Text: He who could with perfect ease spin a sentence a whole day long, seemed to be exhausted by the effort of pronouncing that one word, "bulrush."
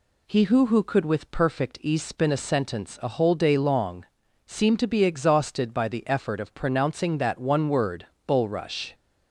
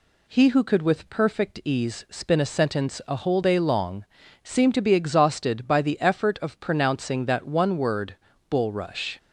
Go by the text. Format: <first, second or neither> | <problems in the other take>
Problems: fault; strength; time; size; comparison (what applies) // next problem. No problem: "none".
second | says "who" twice; at 0.6 s